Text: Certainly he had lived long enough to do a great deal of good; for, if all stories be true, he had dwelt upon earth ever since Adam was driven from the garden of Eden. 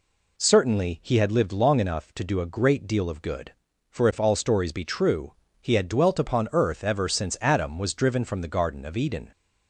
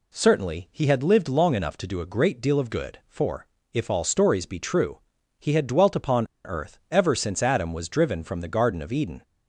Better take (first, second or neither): first